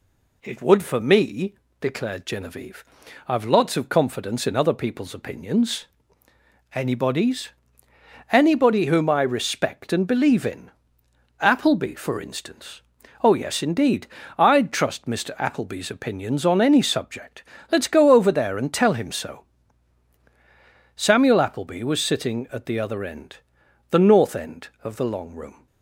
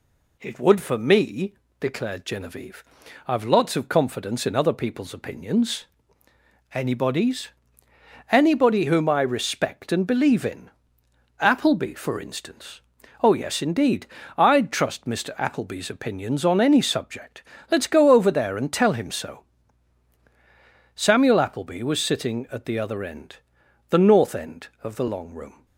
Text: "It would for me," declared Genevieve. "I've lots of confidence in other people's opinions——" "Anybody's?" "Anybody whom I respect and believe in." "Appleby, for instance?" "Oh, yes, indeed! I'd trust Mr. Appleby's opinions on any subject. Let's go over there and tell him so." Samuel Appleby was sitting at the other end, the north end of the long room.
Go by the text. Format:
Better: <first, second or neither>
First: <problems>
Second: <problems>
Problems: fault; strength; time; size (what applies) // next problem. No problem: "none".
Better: neither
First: none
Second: none